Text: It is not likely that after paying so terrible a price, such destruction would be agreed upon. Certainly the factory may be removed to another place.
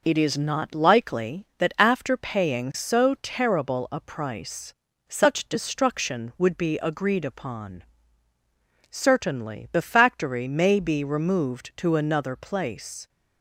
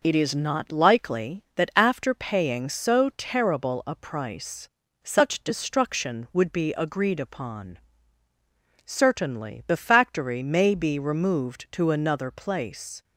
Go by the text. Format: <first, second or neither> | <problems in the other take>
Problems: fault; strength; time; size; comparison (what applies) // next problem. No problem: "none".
neither | none